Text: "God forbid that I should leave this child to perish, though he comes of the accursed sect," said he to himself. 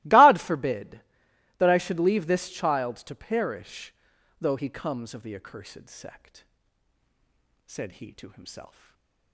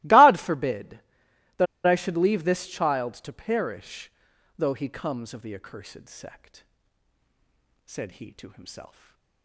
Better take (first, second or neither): first